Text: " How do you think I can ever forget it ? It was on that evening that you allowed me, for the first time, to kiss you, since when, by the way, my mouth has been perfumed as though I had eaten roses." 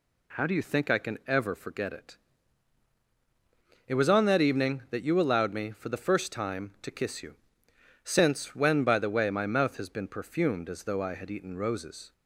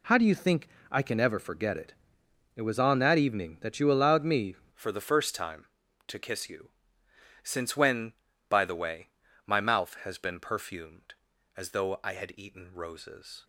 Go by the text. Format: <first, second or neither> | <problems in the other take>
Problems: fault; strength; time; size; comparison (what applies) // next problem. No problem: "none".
first | pauses between "think" and "I"; slight; at 0.6 s; 0.24 s long // changes voice at "for"; from 4.7 s on; 8.7 s long